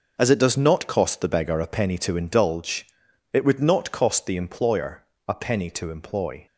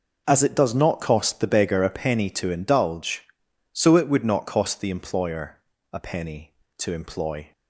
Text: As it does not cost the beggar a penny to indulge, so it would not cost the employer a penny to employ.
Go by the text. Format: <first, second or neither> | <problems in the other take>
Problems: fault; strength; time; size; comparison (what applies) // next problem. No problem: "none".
second | skips "so"; at 3.0 s // pauses between "employer" and "a"; slight; at 5.0 s; 0.24 s long; slight in the second